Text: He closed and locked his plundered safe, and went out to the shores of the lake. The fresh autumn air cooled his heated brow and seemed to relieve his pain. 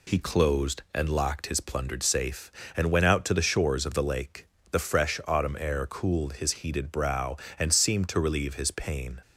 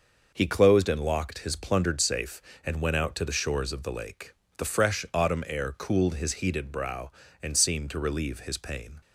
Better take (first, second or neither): neither